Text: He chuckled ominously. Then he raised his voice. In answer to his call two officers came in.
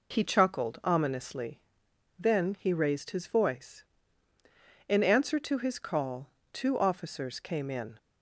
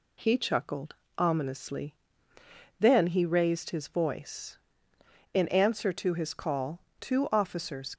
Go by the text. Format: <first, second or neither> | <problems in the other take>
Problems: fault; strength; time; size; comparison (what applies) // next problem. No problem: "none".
first | pauses between "chuckled" and "ominously"; slight; at 0.9 s; 0.22 s long // pauses between "call" and "two"; slight; at 6.8 s; 0.18 s long; slight in the first // stops before "came in"; at 7.9 s